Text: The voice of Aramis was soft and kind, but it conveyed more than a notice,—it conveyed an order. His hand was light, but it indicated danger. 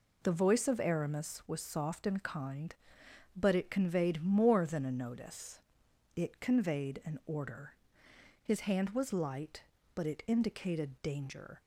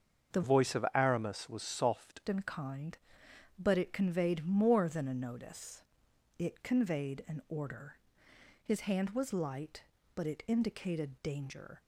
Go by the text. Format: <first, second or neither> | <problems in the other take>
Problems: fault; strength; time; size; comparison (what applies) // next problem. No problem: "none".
first | starts louder than the rest; until 1.4 s; 6.5 dB // changes voice from "voice" to "soft"; from 0.4 to 2.2 s; 1.8 s long